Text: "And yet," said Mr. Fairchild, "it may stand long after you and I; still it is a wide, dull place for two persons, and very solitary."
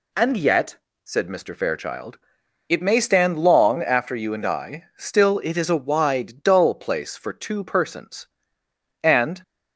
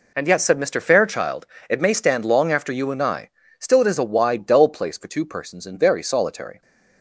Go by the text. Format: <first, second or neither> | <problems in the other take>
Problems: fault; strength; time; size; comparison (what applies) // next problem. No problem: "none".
second | stops before "very solitary"; at 9.4 s